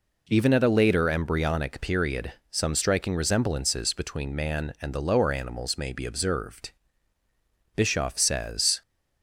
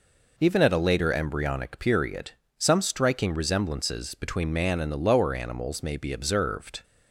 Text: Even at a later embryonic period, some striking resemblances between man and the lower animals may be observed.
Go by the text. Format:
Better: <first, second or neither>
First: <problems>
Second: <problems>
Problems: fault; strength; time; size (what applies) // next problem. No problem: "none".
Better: second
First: goes on to say "Bischoff says"; noticeable; from 7.7 s on; 1.0 s long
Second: none